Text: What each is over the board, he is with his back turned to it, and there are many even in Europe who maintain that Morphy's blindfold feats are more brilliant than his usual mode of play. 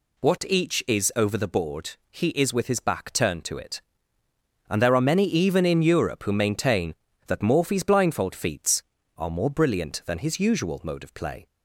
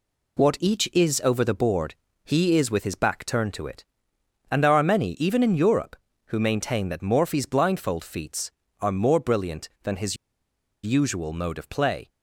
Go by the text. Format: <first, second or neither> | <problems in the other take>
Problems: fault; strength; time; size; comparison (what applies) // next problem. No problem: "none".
first | pauses between "his" and "usual"; noticeable; at 10.1 s; 0.67 s long